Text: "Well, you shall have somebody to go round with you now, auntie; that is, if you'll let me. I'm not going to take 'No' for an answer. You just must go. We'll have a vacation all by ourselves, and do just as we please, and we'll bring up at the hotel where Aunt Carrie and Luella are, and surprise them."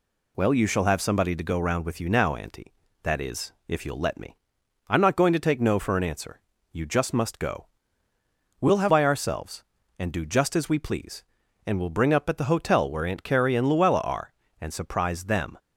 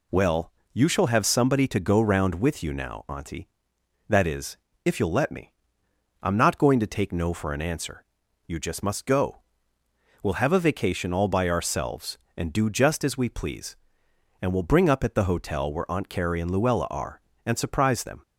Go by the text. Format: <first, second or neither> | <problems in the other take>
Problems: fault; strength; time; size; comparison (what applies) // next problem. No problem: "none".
second | skips "a vacation all"; at 8.8 s